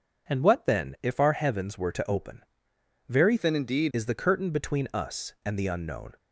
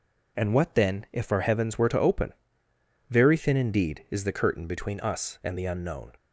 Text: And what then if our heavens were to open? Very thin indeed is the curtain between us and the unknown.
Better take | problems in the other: second | changes voice from "thin" to "indeed"; from 3.3 to 3.9 s; 0.6 s long

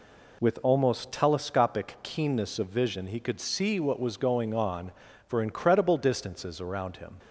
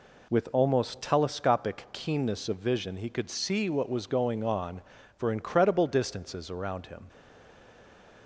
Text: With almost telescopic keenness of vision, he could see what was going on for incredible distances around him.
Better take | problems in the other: first | stays silent after the last word; noticeable; from 7.0 s on; 1.2 s long

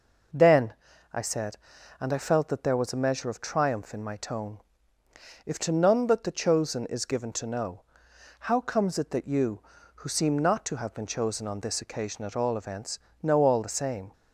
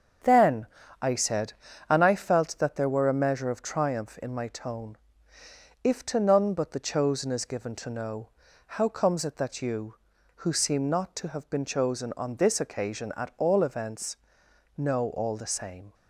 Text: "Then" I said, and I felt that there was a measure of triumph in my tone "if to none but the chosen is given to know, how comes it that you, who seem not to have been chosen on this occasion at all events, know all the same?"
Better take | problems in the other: first | starts louder than the rest; until 1.9 s; 7 dB // pauses between "Then" and "I"; slight; at 0.6 s; 0.34 s long; also in the first // says "were" for "was"; at 2.8 s // pauses between "tone" and "if"; noticeable; at 4.9 s; 0.84 s long; noticeable in the first

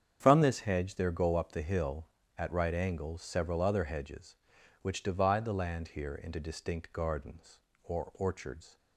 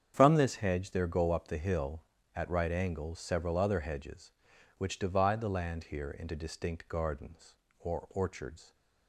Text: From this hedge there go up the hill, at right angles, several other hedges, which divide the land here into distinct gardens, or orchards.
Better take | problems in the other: neither | starts louder than the rest; strong; the same in both

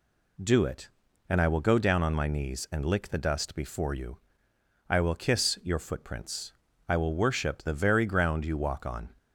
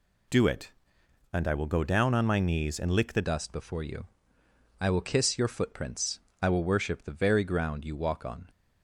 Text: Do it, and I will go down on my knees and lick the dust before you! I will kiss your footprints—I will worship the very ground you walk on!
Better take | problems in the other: first | changes voice at "dust"; from 3.2 s on; 5.2 s long

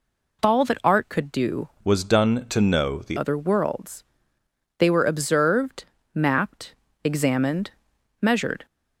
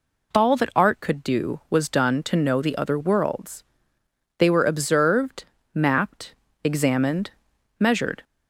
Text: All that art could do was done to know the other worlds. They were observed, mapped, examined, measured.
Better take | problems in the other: second | changes voice from "was" to "the"; from 1.8 to 3.1 s; 1.3 s long

